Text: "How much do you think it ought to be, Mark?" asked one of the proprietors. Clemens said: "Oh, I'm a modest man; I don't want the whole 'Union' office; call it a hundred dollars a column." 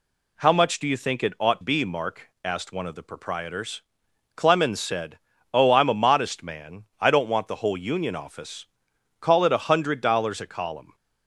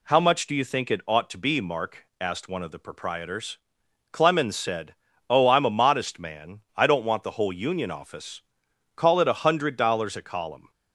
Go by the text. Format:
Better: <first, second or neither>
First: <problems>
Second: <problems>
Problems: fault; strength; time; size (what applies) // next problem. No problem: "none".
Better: second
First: skips "to"; at 1.6 s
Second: none